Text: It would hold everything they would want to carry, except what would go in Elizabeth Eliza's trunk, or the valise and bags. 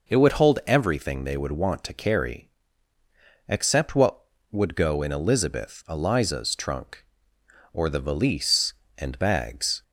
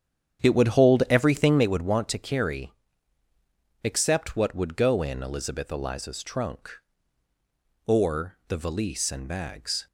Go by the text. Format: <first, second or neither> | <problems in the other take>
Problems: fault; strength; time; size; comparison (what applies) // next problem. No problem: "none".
first | starts louder than the rest; strong; until 1.7 s; 9 dB